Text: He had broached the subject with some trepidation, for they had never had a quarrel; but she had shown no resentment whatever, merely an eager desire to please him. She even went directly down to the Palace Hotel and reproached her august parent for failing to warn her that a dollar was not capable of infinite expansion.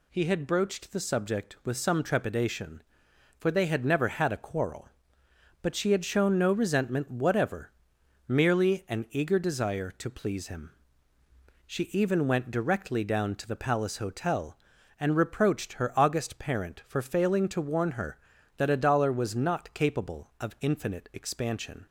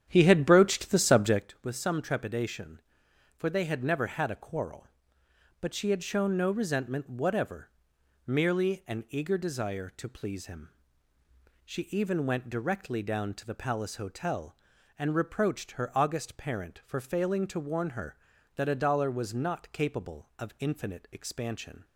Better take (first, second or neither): first